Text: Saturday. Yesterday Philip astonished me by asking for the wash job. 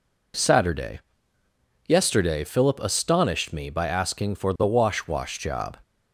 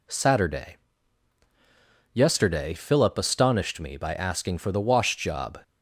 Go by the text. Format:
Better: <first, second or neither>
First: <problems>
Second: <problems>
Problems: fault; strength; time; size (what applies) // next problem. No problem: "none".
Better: second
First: says "wash" twice; at 5.0 s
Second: none